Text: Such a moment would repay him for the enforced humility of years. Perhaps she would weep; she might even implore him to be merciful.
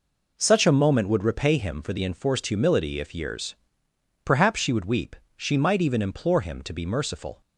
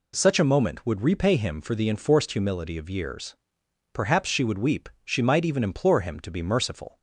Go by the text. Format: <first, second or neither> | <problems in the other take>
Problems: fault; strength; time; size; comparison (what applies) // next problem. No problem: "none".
second | says "if" for "of"; at 2.9 s